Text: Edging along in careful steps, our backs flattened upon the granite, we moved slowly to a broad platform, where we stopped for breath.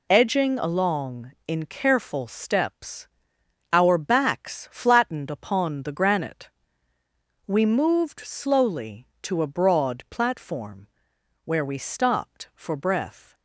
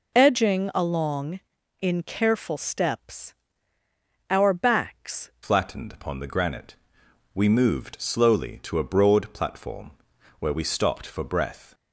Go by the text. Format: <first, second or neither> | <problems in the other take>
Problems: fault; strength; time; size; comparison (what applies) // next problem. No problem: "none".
first | changes voice at "flattened"; from 5.4 s on; 6.3 s long